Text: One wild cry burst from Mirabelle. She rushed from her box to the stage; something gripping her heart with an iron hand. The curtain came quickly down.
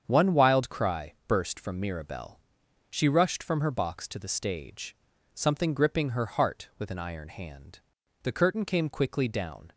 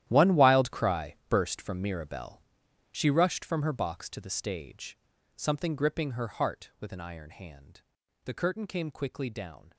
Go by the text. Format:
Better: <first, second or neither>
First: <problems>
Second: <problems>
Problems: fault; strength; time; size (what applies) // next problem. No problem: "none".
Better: first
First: starts louder than the rest; strong; until 1.0 s; 7.5 dB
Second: gets quieter; strong; throughout; 15.5 dB // starts louder than the rest; strong; until 1.0 s; 12 dB